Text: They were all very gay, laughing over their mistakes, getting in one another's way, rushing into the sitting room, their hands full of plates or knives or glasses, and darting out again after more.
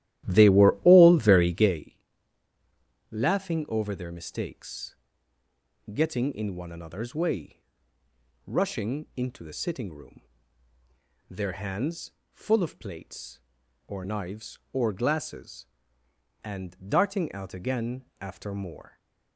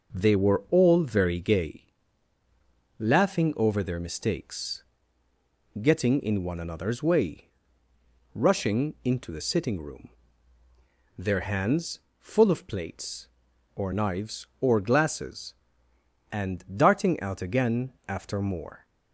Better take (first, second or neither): second